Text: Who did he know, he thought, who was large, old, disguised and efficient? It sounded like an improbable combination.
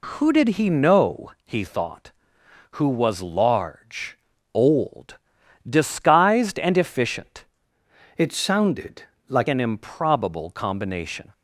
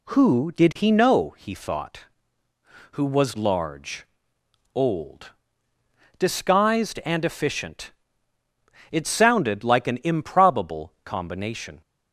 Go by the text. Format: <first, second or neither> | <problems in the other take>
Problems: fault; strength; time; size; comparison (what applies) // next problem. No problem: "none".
second | changes voice from "It" to "like"; from 8.1 to 9.4 s; 1.3 s long // pauses between "sounded" and "like"; slight; at 9.0 s; 0.26 s long